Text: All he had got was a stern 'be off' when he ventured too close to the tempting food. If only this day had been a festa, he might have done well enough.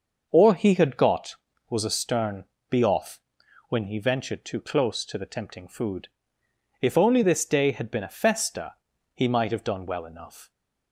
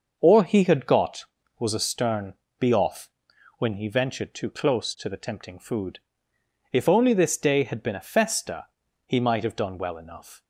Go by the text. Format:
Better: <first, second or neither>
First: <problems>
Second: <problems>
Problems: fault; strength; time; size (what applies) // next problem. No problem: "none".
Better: neither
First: starts louder than the rest; until 1.3 s; 6 dB // pauses between "stern" and "be"; slight; at 2.4 s; 0.26 s long // pauses between "off" and "when"; noticeable; at 3.2 s; 0.48 s long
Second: starts louder than the rest; until 1.1 s; 6 dB // pauses between "stern" and "be"; slight; at 2.3 s; 0.26 s long // pauses between "off" and "when"; noticeable; at 3.1 s; 0.48 s long